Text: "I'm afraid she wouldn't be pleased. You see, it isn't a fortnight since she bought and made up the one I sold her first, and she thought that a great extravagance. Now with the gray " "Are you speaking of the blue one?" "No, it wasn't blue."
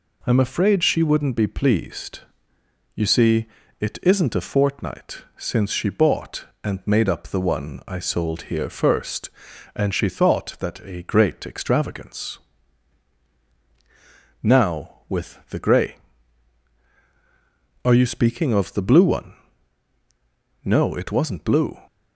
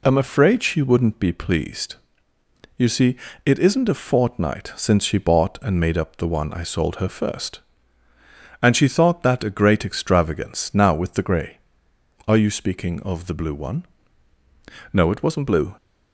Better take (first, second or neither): second